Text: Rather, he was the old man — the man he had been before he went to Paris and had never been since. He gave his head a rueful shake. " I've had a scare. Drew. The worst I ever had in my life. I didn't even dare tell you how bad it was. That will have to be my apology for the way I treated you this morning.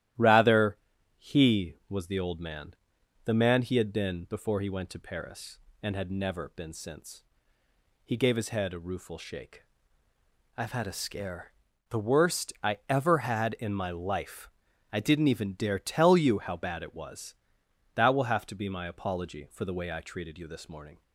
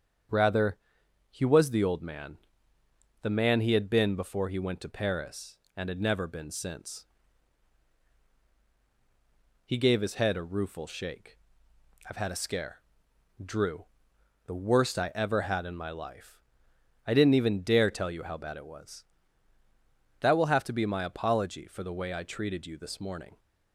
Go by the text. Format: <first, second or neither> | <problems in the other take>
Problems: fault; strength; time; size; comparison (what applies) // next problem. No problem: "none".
second | starts louder than the rest; strong; until 1.5 s; 13.5 dB; strong in the second // skips "Drew"; at 11.7 s